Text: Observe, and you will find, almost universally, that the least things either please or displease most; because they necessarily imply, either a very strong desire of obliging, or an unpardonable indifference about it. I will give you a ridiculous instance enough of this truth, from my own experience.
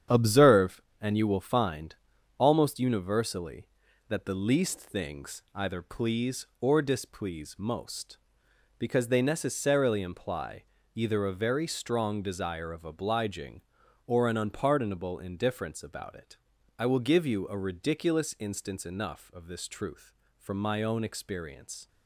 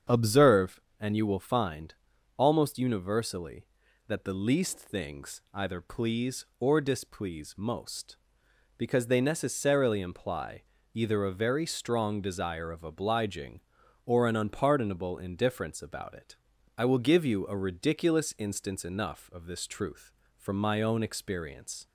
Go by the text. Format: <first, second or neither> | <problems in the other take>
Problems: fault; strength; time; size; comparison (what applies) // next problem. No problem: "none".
second | gets quieter; throughout; 7 dB // starts louder than the rest; strong; until 1.3 s; 8.5 dB; strong in the second